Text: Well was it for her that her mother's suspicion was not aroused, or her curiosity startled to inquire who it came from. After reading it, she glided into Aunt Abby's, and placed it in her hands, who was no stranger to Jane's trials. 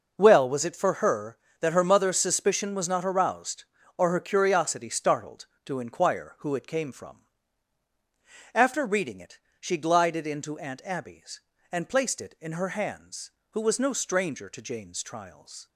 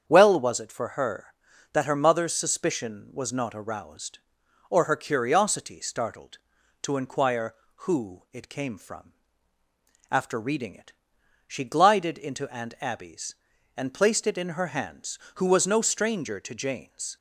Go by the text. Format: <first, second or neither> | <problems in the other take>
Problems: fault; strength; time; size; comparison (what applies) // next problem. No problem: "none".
first | starts louder than the rest; strong; until 1.0 s; 8 dB // stops before "trials"; at 17.1 s